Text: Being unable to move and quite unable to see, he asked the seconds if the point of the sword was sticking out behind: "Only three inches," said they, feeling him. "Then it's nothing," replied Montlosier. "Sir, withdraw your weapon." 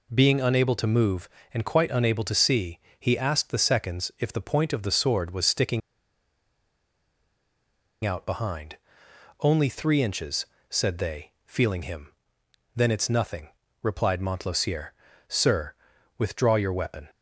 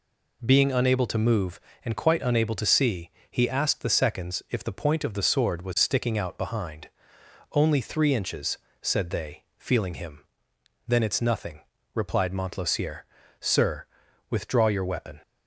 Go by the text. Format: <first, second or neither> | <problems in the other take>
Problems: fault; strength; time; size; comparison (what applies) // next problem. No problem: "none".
second | pauses between "sticking" and "out"; strong; at 5.8 s; 2.2 s long